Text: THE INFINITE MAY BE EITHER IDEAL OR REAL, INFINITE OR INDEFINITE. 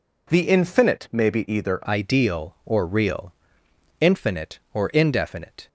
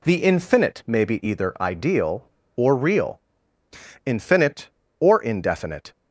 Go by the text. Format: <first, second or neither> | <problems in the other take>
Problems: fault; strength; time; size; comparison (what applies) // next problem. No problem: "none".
second | changes voice at "IDEAL"; from 1.8 s on; 3.8 s long